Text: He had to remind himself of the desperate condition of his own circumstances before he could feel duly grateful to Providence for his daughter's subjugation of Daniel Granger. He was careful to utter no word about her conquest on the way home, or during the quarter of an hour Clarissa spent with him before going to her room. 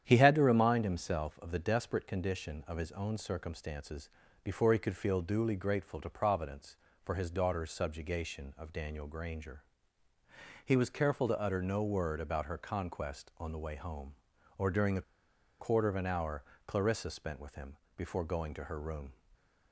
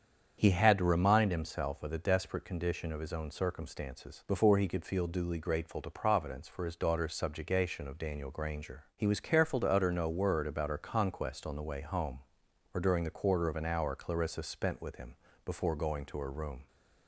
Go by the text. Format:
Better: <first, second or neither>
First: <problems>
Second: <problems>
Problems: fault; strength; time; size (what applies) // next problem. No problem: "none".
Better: second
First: starts louder than the rest; strong; until 1.0 s; 9.5 dB // pauses between "circumstances" and "before"; slight; at 4.0 s; 0.36 s long // pauses between "the" and "quarter"; noticeable; at 15.0 s; 0.57 s long // pauses between "hour" and "Clarissa"; slight; at 16.4 s; 0.24 s long // pauses between "him" and "before"; slight; at 17.7 s; 0.20 s long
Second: starts louder than the rest; strong; until 1.3 s; 7.5 dB // pauses between "him" and "before"; slight; at 15.1 s; 0.28 s long